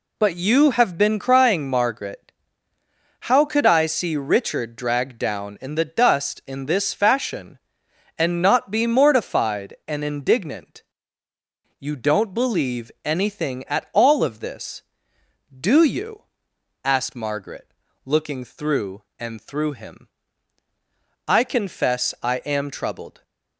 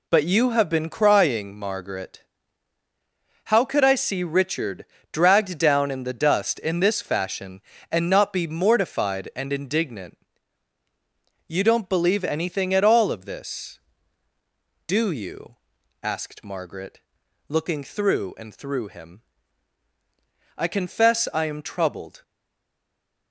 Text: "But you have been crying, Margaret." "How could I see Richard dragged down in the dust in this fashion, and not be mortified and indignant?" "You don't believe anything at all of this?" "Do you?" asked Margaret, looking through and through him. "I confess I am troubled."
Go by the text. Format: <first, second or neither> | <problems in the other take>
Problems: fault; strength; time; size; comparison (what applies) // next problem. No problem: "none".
first | pauses between "Richard" and "dragged"; slight; at 4.8 s; 0.25 s long // stays silent after the last word; from 22.2 s on; 1.1 s long